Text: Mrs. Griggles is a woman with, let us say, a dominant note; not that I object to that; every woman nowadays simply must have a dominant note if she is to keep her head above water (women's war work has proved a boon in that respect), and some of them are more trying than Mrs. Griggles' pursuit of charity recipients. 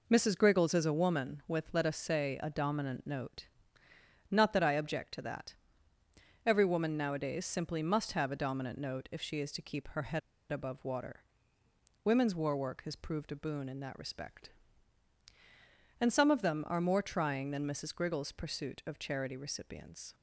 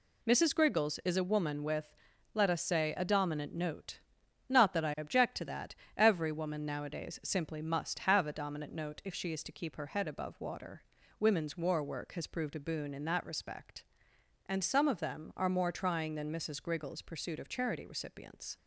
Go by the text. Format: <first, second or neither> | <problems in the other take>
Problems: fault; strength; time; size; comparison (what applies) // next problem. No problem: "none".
second | pauses between "head" and "above"; slight; at 10.2 s; 0.30 s long